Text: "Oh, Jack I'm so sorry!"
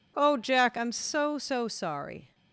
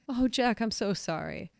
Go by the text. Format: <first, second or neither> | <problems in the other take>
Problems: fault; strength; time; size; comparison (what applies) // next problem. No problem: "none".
second | says "so" twice; at 1.3 s